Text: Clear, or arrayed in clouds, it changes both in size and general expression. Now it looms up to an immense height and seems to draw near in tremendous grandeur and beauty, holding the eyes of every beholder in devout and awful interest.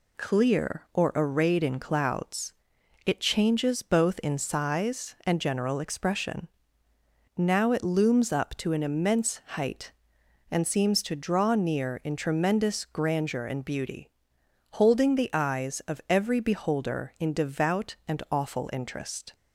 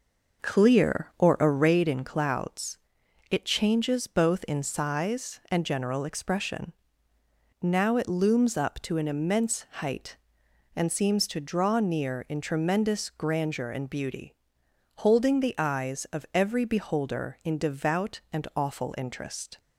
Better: first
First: none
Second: starts louder than the rest; noticeable; until 2.0 s; 6 dB

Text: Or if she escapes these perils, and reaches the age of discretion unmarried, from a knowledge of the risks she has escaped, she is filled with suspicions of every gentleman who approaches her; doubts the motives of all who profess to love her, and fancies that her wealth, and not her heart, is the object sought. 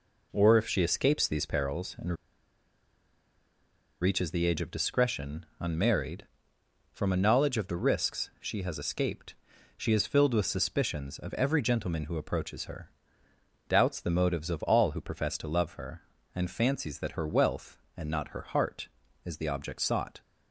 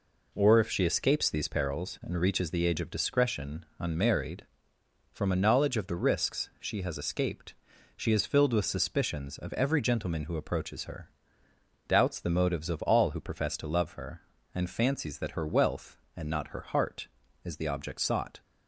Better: second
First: pauses between "and" and "reaches"; strong; at 2.1 s; 1.8 s long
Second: none

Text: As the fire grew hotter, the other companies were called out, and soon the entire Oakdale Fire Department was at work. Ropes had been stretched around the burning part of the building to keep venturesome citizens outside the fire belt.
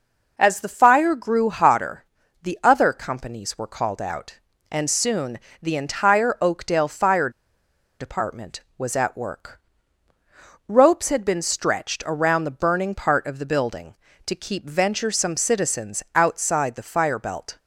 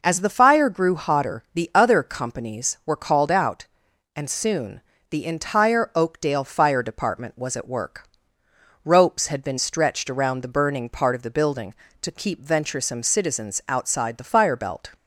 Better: second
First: pauses between "soon" and "the"; slight; at 5.3 s; 0.24 s long // pauses between "Fire" and "Department"; noticeable; at 7.3 s; 0.69 s long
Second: pauses between "soon" and "the"; slight; at 4.8 s; 0.30 s long

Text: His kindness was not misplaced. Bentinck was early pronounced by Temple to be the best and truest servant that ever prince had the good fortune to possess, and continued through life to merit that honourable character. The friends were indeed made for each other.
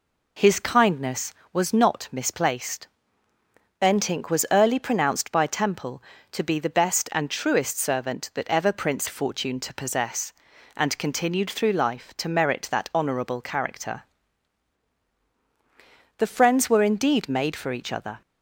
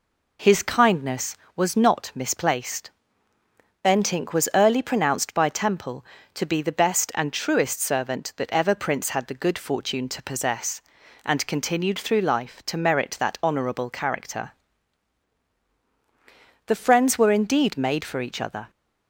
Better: second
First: skips "had the good"; at 9.0 s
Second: none

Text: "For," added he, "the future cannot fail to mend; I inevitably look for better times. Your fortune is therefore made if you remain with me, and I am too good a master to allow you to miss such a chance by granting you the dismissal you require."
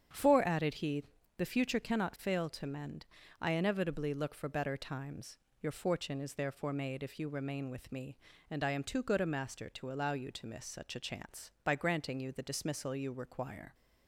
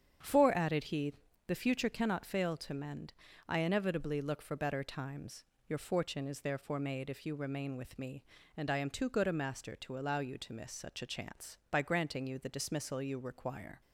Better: neither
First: starts louder than the rest; strong; until 1.4 s; 8 dB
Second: starts louder than the rest; strong; until 1.5 s; 8 dB

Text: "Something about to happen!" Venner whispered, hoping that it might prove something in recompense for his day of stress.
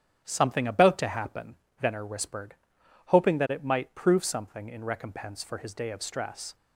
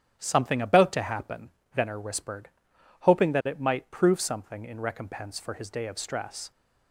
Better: neither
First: starts louder than the rest; strong; until 1.2 s; 9 dB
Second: starts louder than the rest; strong; until 1.1 s; 9 dB

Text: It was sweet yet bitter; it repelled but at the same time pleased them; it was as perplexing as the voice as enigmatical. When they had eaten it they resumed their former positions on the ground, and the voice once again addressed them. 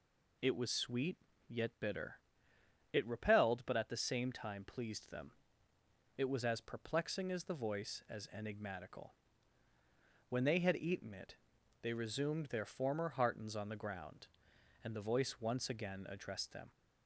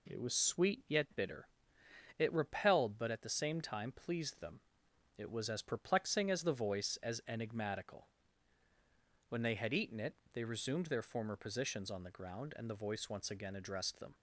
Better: second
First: pauses between "sweet" and "yet"; slight; at 1.1 s; 0.32 s long // pauses between "it" and "they"; noticeable; at 11.3 s; 0.46 s long // says "heartens" for "positions"; at 13.0 s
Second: pauses between "it" and "they"; slight; at 10.1 s; 0.16 s long

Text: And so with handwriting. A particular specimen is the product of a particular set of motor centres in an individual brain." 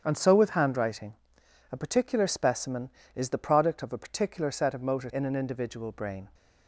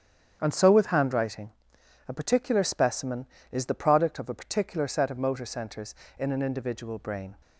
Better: second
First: starts louder than the rest; strong; until 1.0 s; 8 dB // skips "centres"; at 5.1 s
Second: starts louder than the rest; strong; until 1.4 s; 8.5 dB

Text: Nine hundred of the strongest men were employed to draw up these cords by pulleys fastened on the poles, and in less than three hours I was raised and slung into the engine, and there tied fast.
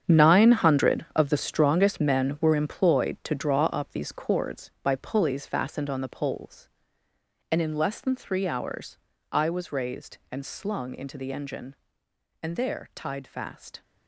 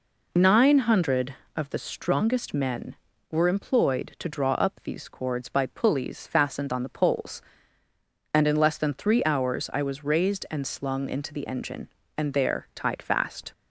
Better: second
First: gets quieter; strong; throughout; 12.5 dB // pauses between "hours" and "I"; slight; at 8.9 s; 0.34 s long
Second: none

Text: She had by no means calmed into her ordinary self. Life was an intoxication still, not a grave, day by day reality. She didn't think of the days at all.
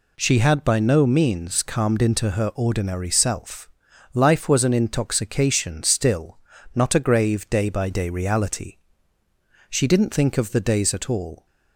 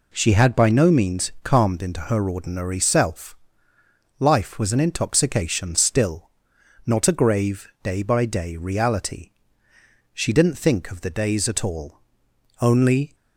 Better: first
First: none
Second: goes on to say "Only"; from 12.6 s on; 0.54 s long

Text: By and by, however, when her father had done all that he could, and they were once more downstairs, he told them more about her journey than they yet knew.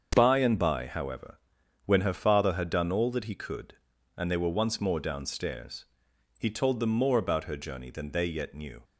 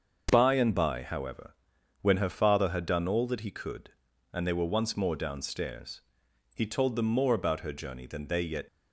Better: first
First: starts louder than the rest; until 1.1 s; 7 dB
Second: starts louder than the rest; until 1.3 s; 6.5 dB // stops before "knew"; at 8.6 s

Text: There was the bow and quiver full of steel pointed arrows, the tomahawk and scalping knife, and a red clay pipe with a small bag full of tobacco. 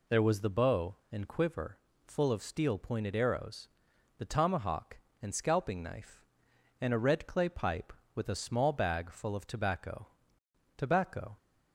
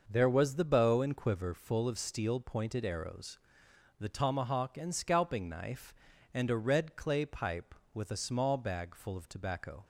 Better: second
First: pauses between "quiver" and "full"; slight; at 1.7 s; 0.26 s long // says "tobacco" twice; at 10.7 s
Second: none

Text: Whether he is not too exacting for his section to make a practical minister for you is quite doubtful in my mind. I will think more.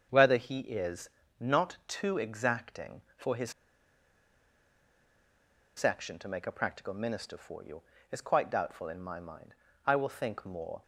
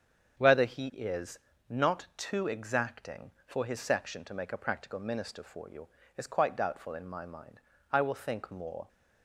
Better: second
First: starts louder than the rest; strong; until 1.1 s; 7.5 dB // pauses between "is" and "not"; slight; at 1.1 s; 0.28 s long // pauses between "his" and "section"; strong; at 3.5 s; 2.2 s long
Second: starts louder than the rest; strong; until 1.7 s; 7.5 dB // pauses between "is" and "not"; slight; at 1.3 s; 0.28 s long

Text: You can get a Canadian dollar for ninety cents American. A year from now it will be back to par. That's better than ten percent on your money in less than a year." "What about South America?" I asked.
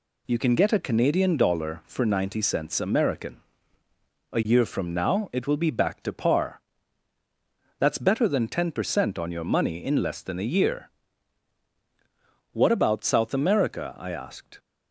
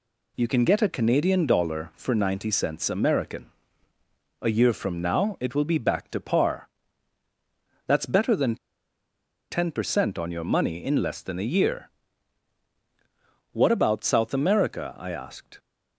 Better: first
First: none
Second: pauses between "than" and "ten"; noticeable; at 8.5 s; 0.94 s long

